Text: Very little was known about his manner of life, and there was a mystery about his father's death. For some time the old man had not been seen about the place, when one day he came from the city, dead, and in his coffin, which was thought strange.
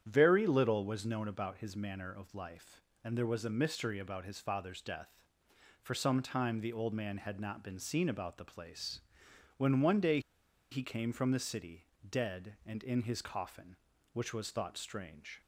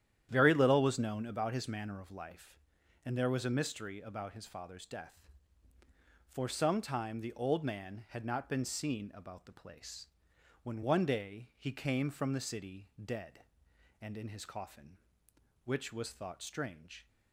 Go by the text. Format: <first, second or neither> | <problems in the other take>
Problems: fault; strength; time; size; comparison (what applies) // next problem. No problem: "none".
second | starts louder than the rest; strong; until 1.0 s; 9 dB; strong in the second // pauses between "day" and "he"; noticeable; at 10.1 s; 0.52 s long